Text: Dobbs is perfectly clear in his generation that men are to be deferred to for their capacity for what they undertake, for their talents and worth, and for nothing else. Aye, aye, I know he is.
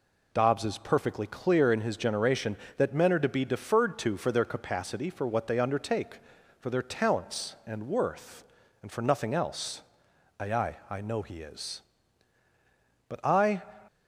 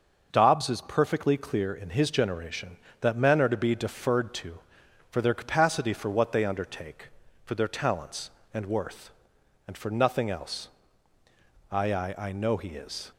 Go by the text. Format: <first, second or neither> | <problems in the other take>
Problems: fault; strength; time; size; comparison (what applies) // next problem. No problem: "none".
second | goes on to say "But I"; from 13.0 s on; 0.54 s long